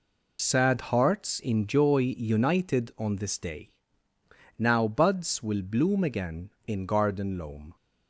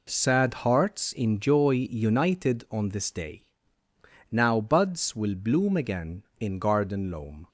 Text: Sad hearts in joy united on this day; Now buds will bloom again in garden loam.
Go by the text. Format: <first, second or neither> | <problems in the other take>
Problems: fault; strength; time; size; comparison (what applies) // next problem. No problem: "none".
second | loses the start of "Sad"; at 0.3 s; 50 ms